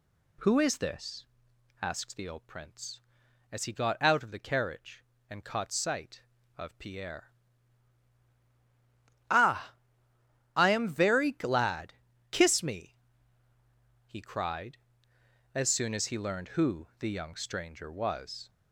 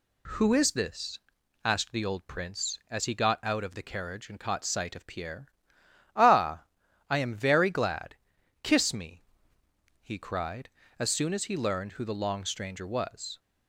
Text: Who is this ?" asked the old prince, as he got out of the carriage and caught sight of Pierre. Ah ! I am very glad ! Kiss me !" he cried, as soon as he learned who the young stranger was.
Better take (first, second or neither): first